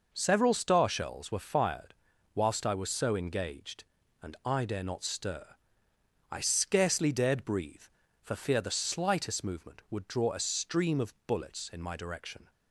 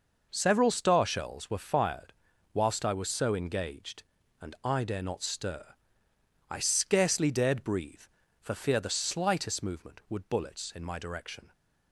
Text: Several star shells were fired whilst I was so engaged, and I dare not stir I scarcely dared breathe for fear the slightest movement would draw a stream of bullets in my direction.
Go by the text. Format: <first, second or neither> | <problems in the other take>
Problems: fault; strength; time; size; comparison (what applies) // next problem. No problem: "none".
first | pauses between "fired" and "whilst"; at 2.1 s; 0.40 s long; also in the first // pauses between "stir" and "I"; noticeable; at 5.6 s; 0.84 s long; noticeable in the first // skips "draw a stream of"; at 10.2 s